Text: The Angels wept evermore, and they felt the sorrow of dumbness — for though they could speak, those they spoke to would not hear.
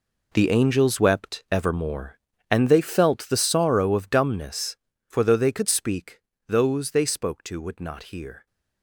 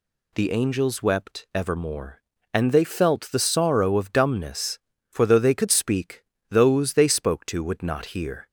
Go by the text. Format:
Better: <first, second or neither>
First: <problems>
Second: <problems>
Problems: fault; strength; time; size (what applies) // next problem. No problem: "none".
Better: second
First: gets quieter; strong; throughout; 13 dB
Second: none